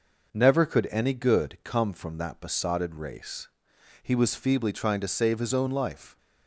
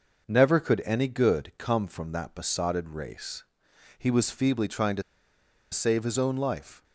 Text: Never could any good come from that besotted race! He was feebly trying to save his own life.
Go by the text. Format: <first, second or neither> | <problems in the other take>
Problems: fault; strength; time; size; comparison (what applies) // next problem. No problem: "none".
first | pauses between "to" and "save"; noticeable; at 5.0 s; 0.69 s long